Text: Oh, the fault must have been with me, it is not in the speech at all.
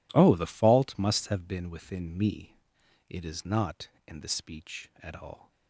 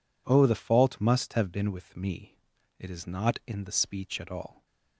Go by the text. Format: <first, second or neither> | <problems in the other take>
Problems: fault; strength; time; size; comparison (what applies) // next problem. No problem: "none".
second | says "within" for "with"; at 1.7 s